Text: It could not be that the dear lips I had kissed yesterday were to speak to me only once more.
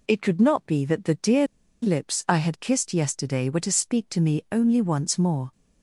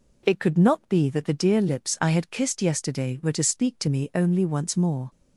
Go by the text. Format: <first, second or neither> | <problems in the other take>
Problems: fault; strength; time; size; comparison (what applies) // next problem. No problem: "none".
second | pauses between "dear" and "lips"; at 1.4 s; 0.36 s long